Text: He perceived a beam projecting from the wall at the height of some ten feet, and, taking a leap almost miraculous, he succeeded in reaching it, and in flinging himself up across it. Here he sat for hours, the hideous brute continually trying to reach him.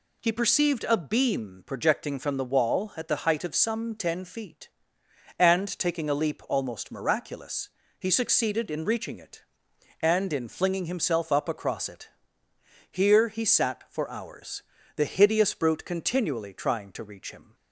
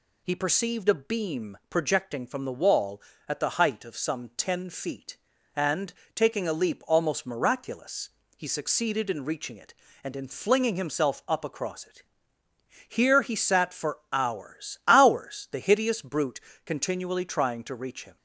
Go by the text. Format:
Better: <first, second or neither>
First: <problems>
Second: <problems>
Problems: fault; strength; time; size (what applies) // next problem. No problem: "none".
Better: first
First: none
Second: says "hours" twice; at 14.8 s // pauses between "brute" and "continually"; slight; at 16.4 s; 0.24 s long